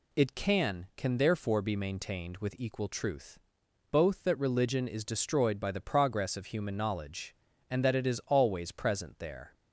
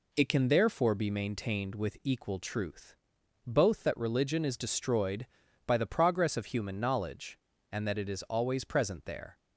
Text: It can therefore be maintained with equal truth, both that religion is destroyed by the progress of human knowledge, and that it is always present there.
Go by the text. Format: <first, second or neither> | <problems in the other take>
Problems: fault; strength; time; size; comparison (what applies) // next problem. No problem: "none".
second | says "can" twice; at 0.9 s